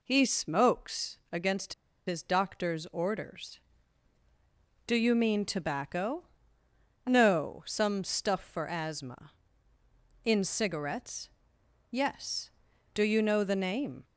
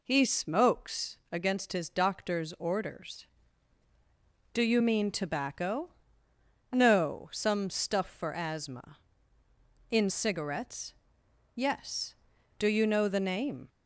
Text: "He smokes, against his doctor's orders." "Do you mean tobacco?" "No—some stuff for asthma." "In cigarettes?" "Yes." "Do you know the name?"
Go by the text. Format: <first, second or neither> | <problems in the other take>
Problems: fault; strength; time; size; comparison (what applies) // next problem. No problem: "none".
second | pauses between "against" and "his"; slight; at 1.7 s; 0.33 s long